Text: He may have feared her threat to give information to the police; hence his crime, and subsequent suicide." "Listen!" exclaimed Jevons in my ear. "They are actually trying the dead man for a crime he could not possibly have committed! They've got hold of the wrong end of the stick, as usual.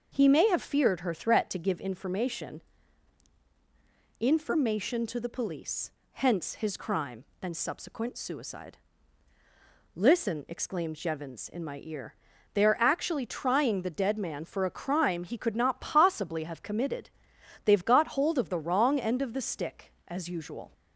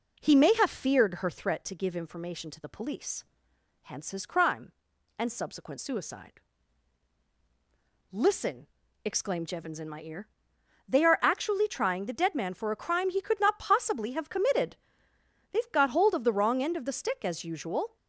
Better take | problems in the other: second | says "information" twice; at 4.2 s

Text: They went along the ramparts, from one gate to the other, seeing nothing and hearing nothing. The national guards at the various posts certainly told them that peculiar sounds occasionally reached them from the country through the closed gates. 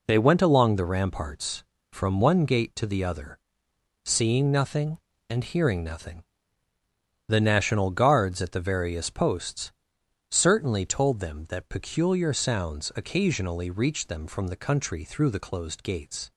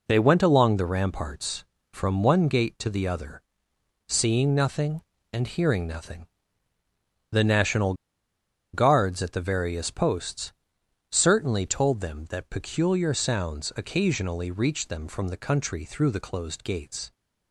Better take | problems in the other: first | pauses between "national" and "guards"; noticeable; at 7.9 s; 0.79 s long // pauses between "posts" and "certainly"; noticeable; at 10.5 s; 0.58 s long; noticeable in the first

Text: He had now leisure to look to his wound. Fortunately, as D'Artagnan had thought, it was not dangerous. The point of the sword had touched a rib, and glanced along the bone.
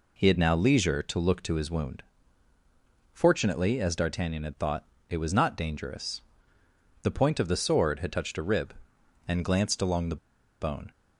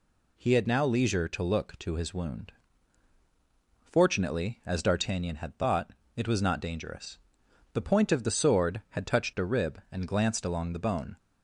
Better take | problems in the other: second | pauses between "the" and "bone"; at 10.1 s; 0.44 s long

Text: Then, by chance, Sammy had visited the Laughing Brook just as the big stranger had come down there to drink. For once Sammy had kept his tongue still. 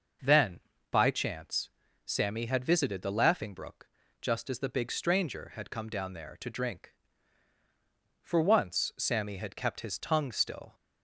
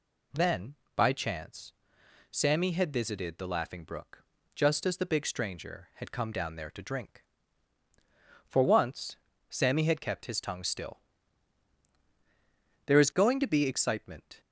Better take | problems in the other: first | pauses between "Brook" and "just"; slight; at 4.2 s; 0.30 s long; slight in the first // pauses between "once" and "Sammy"; slight; at 9.1 s; 0.32 s long // goes on to say "There is going to be excitement"; from 12.8 s on; 1.5 s long

